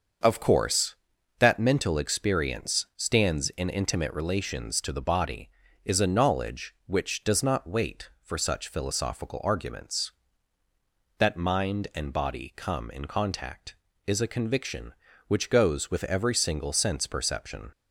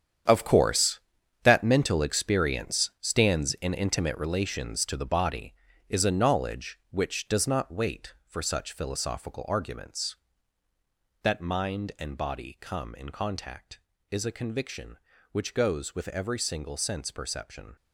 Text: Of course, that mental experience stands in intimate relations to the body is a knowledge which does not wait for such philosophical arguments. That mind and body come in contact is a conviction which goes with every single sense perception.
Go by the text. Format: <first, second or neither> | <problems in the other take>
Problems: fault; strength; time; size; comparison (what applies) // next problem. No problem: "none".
first | gets quieter; strong; throughout; 12 dB // starts louder than the rest; strong; until 1.7 s; 8.5 dB; also in the first